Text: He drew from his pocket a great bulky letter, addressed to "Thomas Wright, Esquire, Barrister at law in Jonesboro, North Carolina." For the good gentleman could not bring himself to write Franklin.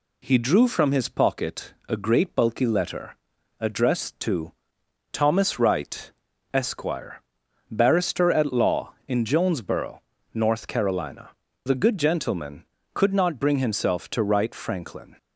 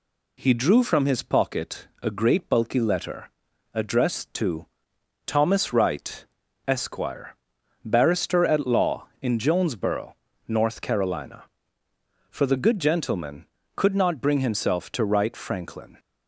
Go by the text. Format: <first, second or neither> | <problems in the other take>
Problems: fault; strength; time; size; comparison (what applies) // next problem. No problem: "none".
second | pauses between "pocket" and "a"; slight; at 1.7 s; 0.16 s long; slight in the second // pauses between "to" and "Thomas"; noticeable; at 4.5 s; 0.58 s long; noticeable in the second // skips "For"; at 11.4 s